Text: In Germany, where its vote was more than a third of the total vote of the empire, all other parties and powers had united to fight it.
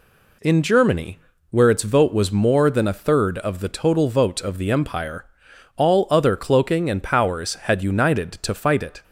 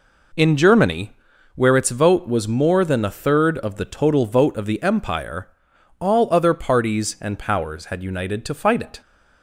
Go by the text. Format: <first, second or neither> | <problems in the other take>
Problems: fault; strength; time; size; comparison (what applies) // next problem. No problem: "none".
second | says "cloaking" for "parties"; at 6.3 s